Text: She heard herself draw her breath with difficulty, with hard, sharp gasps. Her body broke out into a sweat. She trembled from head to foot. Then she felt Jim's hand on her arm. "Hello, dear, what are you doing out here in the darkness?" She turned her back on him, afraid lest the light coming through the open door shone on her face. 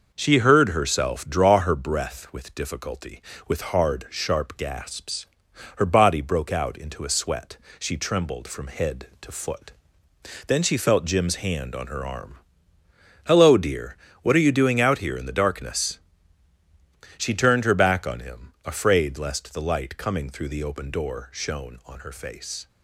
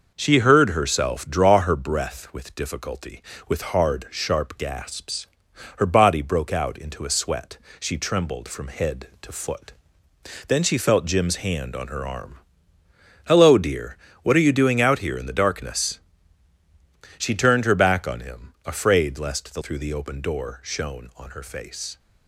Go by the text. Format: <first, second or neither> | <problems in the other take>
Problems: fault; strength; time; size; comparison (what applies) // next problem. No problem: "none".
first | skips "light coming"; at 19.6 s